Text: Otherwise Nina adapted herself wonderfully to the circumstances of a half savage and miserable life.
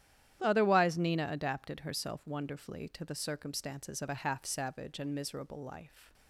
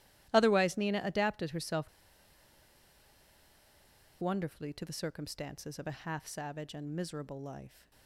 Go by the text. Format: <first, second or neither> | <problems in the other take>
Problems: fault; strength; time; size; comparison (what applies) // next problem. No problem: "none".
first | starts louder than the rest; strong; until 1.3 s; 14 dB; strong in the first // pauses between "herself" and "wonderfully"; strong; at 1.8 s; 2.3 s long